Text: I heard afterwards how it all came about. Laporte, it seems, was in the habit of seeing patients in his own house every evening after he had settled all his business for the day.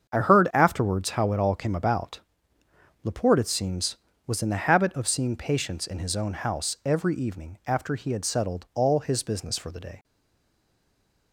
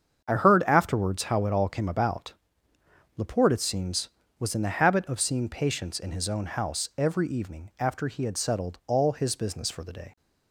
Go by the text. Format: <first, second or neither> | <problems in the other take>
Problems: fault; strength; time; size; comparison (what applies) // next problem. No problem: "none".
second | starts louder than the rest; strong; until 1.1 s; 7 dB; strong in the second // stays silent after the last word; noticeable; from 10.0 s on; 1.3 s long